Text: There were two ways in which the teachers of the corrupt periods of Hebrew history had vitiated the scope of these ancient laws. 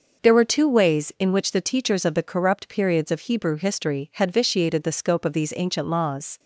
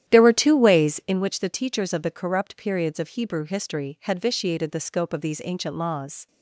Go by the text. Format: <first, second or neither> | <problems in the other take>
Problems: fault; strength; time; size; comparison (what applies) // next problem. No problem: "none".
first | starts louder than the rest; strong; until 1.2 s; 11 dB